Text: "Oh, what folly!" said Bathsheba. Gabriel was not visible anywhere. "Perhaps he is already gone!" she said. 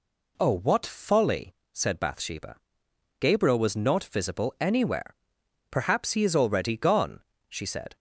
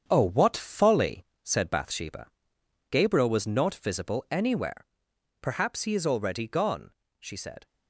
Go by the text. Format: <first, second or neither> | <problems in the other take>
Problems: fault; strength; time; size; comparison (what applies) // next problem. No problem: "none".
first | gets quieter; throughout; 6.5 dB